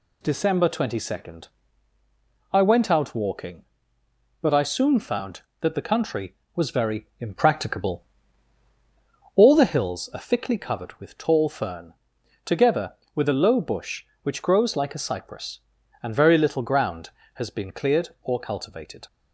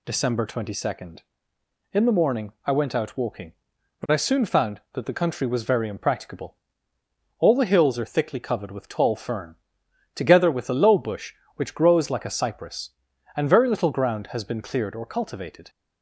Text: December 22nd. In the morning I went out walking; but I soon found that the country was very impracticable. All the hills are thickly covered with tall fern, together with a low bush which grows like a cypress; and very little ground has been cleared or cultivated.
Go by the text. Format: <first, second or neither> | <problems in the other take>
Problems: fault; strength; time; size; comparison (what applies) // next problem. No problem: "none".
second | skips "In the morning"; at 1.9 s